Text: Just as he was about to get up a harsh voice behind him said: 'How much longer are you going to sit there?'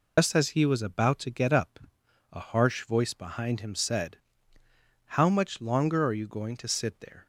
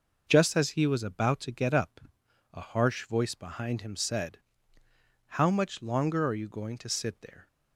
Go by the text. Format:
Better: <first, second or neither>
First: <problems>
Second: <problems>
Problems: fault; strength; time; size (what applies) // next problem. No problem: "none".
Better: second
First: loses the start of "Just"; at 0.1 s; 100 ms // pauses between "up" and "a"; noticeable; at 1.7 s; 0.52 s long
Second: pauses between "up" and "a"; noticeable; at 2.0 s; 0.52 s long